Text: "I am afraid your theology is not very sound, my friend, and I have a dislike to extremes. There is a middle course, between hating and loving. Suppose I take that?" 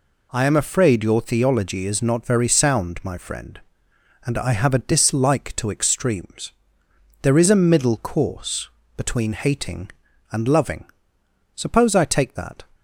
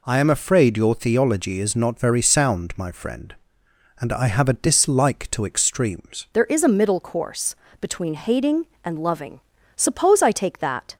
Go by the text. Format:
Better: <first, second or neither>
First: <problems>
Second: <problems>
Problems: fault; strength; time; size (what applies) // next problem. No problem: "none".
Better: first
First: none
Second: changes voice at "There"; from 6.3 s on; 4.6 s long